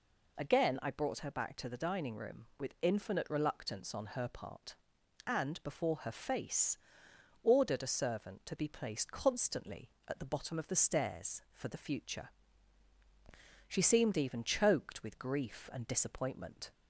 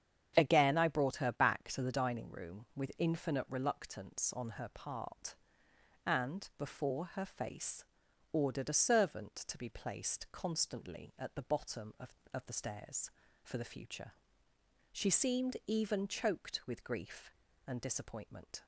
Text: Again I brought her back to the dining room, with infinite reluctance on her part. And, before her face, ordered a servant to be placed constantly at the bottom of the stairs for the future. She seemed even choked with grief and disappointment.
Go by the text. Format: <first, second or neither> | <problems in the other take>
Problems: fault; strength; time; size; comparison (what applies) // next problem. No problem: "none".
first | starts louder than the rest; strong; until 1.3 s; 8 dB // says "of" twice; at 12.3 s